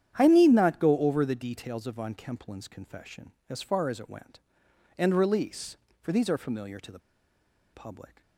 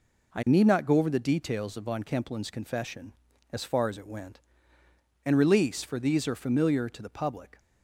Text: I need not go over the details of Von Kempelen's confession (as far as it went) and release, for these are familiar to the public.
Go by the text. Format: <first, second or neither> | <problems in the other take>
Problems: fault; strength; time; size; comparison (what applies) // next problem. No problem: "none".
second | starts louder than the rest; strong; until 1.1 s; 9.5 dB // pauses between "the" and "public"; noticeable; at 7.0 s; 0.73 s long